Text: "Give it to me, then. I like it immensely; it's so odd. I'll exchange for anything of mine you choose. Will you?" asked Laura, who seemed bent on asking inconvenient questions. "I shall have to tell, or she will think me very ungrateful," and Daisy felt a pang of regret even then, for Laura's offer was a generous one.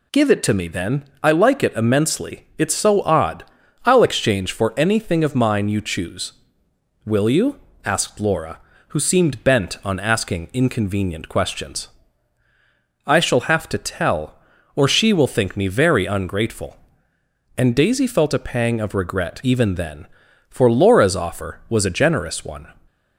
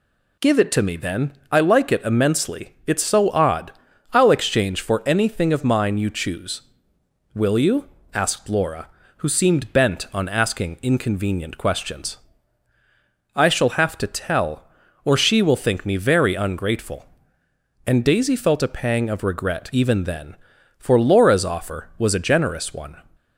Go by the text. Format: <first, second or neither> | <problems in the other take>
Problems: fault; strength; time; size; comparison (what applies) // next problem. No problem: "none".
neither | none